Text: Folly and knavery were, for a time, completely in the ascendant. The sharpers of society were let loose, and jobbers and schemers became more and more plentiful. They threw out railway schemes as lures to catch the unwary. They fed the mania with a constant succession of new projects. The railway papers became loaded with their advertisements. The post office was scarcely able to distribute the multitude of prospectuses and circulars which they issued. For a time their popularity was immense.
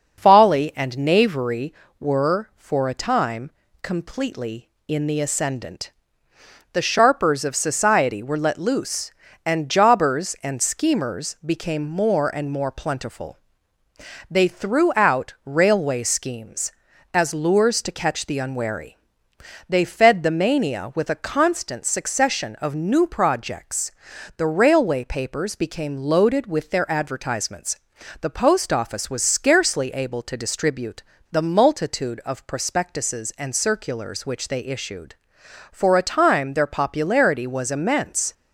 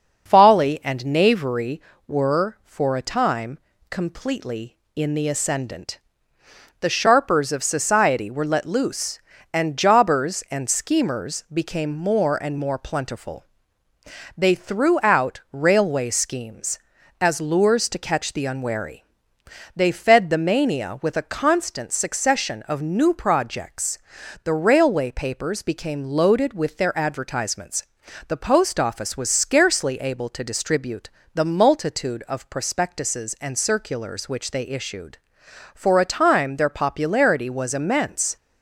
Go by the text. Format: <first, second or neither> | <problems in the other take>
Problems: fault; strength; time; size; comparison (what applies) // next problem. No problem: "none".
neither | starts louder than the rest; noticeable; the same in both // pauses between "distribute" and "the"; slight; the same in both